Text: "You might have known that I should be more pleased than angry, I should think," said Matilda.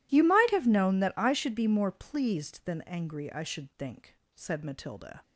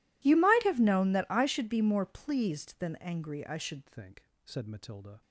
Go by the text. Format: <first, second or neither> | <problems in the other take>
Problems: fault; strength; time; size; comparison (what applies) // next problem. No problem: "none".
first | changes voice at "think"; from 3.8 s on; 1.4 s long